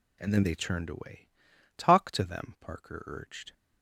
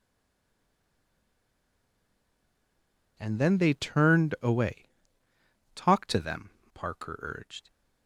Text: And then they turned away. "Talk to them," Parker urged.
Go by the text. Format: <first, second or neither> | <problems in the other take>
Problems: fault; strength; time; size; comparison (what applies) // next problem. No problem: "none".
first | stays silent before the first word; strong; until 3.1 s; 3.1 s long